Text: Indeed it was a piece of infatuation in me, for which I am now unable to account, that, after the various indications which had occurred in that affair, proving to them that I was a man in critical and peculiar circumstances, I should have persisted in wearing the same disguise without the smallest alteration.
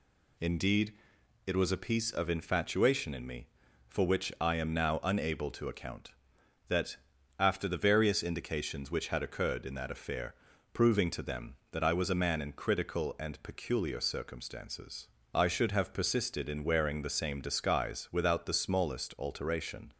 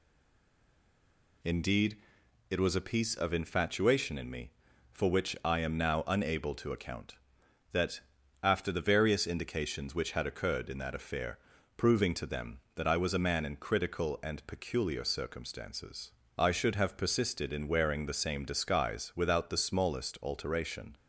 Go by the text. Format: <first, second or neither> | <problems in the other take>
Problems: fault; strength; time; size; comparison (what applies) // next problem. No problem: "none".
first | stays silent before the first word; noticeable; until 1.4 s; 1.4 s long // pauses between "Indeed" and "it"; noticeable; at 1.9 s; 0.52 s long; noticeable in the first